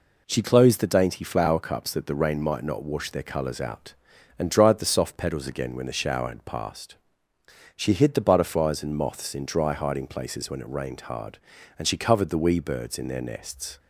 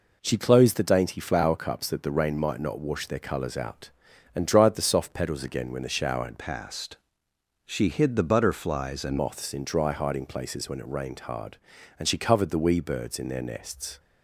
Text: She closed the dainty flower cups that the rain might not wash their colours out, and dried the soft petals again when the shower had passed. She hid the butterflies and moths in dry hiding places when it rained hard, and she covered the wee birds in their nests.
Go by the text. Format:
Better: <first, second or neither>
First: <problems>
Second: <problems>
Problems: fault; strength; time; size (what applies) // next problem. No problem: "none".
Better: first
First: none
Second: changes voice from "passed" to "and"; from 6.3 to 9.1 s; 2.8 s long